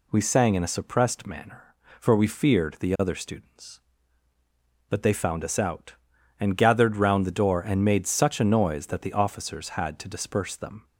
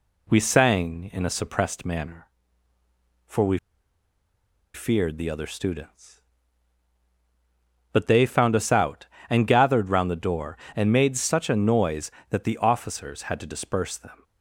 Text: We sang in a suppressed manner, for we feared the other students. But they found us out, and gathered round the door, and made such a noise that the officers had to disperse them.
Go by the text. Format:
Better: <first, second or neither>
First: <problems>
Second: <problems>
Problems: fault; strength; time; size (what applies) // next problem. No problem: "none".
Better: first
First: none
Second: pauses between "we" and "feared"; at 3.5 s; 1.1 s long